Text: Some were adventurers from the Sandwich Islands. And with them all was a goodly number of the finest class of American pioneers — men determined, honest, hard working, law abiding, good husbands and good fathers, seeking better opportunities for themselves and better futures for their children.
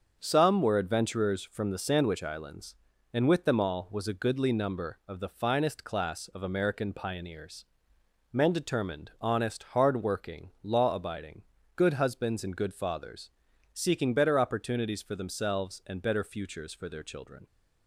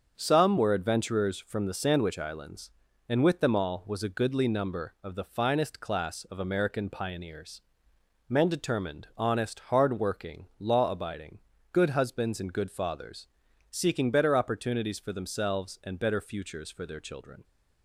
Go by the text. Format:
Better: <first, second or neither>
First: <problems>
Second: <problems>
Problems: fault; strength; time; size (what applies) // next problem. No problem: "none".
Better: neither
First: starts louder than the rest; until 1.2 s; 6.5 dB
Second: starts louder than the rest; until 1.1 s; 6.5 dB